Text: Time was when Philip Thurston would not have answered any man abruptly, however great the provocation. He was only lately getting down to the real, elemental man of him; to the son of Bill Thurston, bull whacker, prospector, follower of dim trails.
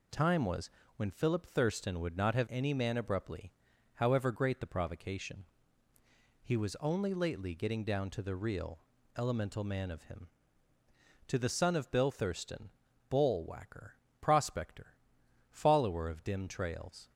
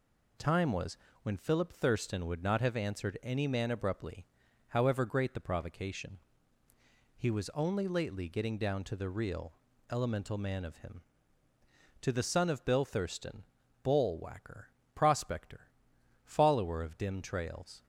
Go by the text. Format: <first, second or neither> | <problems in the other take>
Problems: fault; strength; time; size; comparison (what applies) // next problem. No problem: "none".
second | pauses between "was" and "when"; slight; at 0.6 s; 0.28 s long; slight in the second // skips "answered"; at 2.4 s